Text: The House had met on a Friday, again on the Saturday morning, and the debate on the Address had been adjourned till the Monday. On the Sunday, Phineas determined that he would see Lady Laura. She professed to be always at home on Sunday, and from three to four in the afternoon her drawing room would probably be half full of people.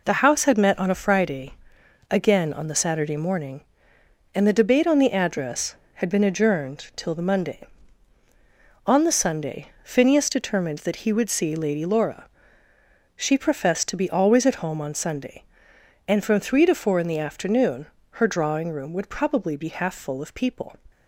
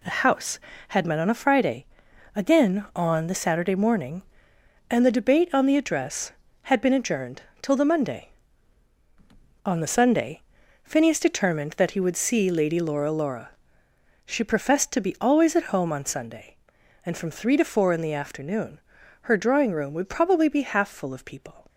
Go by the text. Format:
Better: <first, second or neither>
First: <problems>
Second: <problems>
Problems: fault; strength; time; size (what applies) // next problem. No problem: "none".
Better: first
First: pauses between "afternoon" and "her"; slight; at 17.8 s; 0.24 s long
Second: pauses between "adjourned" and "till"; slight; at 7.4 s; 0.18 s long // says "Laura" twice; at 13.1 s // pauses between "afternoon" and "her"; at 18.8 s; 0.42 s long